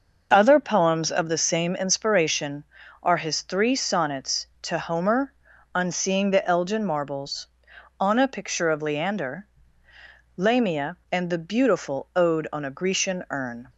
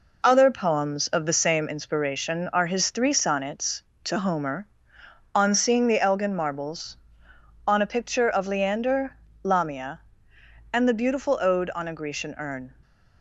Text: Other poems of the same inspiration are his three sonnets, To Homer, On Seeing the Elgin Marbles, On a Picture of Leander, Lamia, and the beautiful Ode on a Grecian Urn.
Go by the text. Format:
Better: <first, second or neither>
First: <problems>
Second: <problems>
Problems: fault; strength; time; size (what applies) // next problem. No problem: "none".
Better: neither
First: none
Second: none